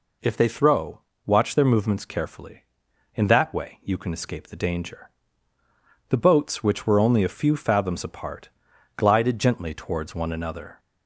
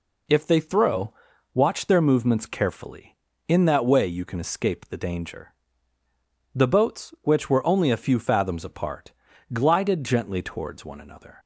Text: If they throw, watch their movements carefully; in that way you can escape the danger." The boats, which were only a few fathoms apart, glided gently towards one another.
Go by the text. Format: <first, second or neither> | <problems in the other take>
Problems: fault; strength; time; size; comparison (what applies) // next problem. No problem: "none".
neither | none